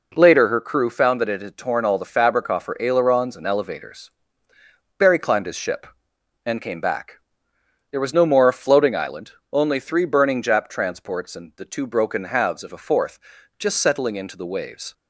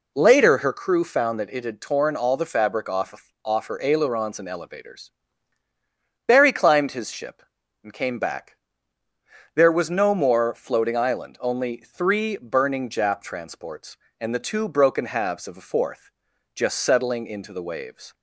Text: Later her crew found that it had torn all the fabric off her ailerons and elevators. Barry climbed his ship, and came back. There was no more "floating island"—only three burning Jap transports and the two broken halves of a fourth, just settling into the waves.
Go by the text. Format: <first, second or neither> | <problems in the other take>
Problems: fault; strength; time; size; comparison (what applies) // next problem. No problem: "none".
first | says "off" twice; at 3.4 s